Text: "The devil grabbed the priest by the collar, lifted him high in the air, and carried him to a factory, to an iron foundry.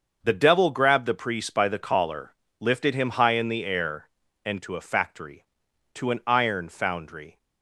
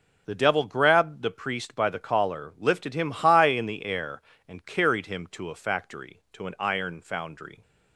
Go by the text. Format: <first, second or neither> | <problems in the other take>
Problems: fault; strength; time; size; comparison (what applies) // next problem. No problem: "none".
second | starts louder than the rest; until 1.2 s; 6.5 dB // skips "carried him"; at 4.6 s